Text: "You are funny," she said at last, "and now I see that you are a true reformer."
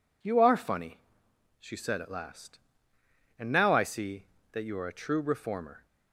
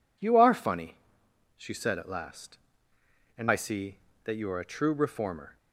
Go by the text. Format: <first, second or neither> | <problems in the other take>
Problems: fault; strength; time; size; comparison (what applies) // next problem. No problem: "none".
first | skips "now"; at 3.4 s